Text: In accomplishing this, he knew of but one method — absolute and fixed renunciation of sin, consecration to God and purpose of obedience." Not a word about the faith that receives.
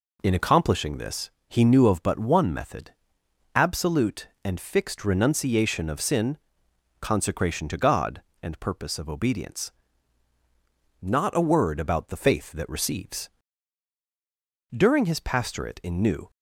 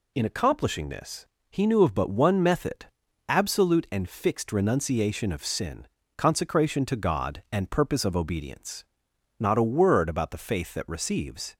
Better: second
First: goes on to say "During his pastorate in New"; from 14.7 s on; 1.5 s long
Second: none

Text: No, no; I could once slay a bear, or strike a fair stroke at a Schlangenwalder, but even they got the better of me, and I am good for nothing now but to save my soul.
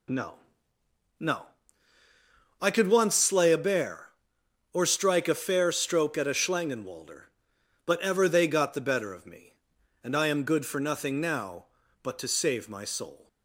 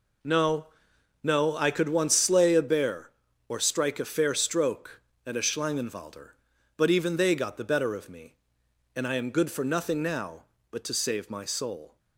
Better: second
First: says "ever" for "even"; at 7.9 s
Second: none

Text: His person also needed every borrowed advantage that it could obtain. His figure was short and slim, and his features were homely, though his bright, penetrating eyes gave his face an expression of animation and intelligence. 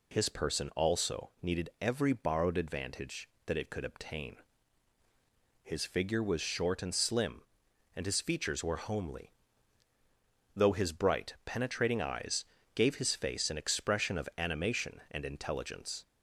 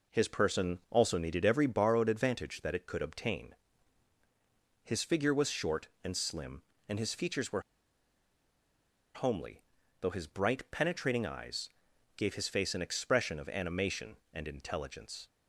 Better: first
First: pauses between "eyes" and "gave"; slight; at 12.4 s; 0.28 s long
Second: pauses between "were" and "homely"; strong; at 7.6 s; 1.5 s long // pauses between "eyes" and "gave"; noticeable; at 11.6 s; 0.46 s long

